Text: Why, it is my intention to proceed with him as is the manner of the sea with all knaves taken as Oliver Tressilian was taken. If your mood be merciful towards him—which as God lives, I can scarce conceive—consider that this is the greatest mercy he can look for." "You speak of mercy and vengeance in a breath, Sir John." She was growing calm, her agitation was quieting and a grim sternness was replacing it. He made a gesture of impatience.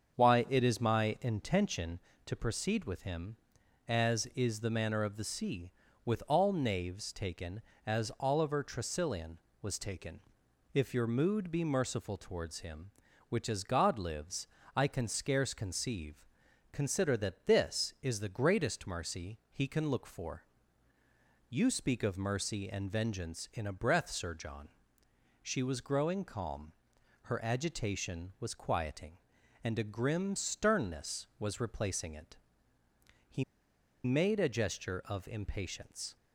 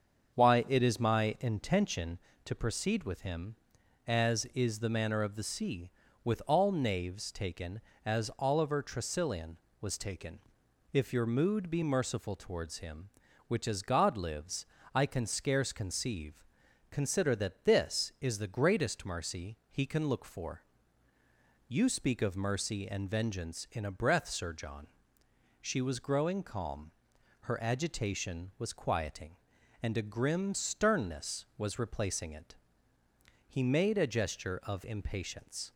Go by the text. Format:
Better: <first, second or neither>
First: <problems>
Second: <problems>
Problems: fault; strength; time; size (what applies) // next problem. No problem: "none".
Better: second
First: starts louder than the rest; until 1.1 s; 7 dB // pauses between "He" and "made"; noticeable; at 33.4 s; 0.61 s long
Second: starts louder than the rest; until 1.4 s; 7 dB